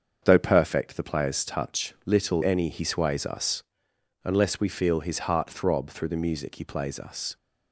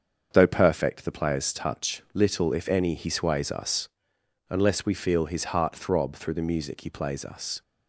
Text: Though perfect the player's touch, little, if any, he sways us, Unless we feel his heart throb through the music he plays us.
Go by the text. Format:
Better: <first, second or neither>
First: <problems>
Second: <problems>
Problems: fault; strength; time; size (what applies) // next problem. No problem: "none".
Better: second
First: starts louder than the rest; until 1.2 s; 7 dB // skips "if"; at 2.4 s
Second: starts louder than the rest; until 1.3 s; 7 dB